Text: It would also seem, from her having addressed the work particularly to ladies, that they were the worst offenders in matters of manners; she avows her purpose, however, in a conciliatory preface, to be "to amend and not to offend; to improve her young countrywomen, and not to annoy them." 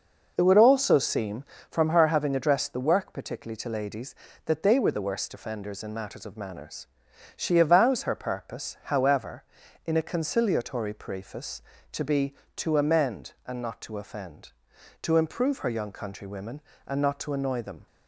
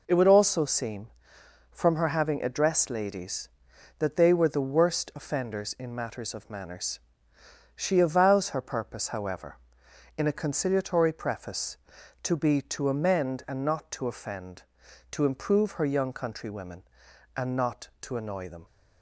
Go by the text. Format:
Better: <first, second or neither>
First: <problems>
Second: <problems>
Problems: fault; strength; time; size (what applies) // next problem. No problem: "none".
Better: first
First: none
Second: skips "the work particularly to"; at 2.8 s